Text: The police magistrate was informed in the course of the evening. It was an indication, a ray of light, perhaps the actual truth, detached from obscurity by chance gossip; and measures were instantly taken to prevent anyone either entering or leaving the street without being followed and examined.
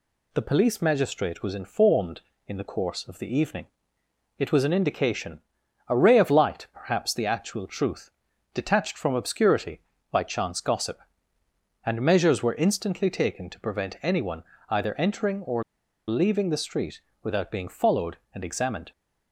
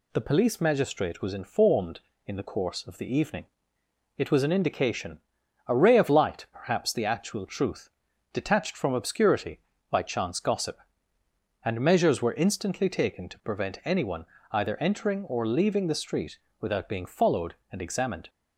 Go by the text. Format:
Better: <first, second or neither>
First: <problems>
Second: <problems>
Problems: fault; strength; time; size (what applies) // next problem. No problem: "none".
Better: second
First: pauses between "anyone" and "either"; slight; at 14.4 s; 0.24 s long // pauses between "or" and "leaving"; noticeable; at 15.6 s; 0.46 s long // pauses between "street" and "without"; slight; at 16.9 s; 0.24 s long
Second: pauses between "anyone" and "either"; slight; at 14.2 s; 0.24 s long // pauses between "street" and "without"; slight; at 16.3 s; 0.24 s long